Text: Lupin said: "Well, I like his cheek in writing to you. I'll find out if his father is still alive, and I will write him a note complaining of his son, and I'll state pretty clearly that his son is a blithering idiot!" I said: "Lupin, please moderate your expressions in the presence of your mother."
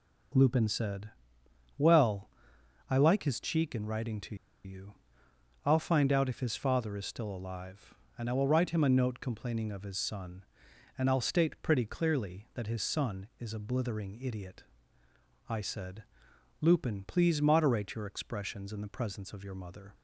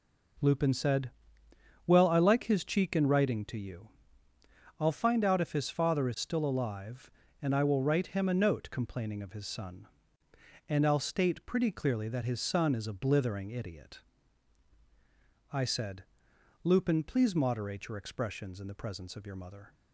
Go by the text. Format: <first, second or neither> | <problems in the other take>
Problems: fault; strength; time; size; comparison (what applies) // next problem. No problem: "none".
second | pauses between "to" and "you"; slight; at 4.3 s; 0.29 s long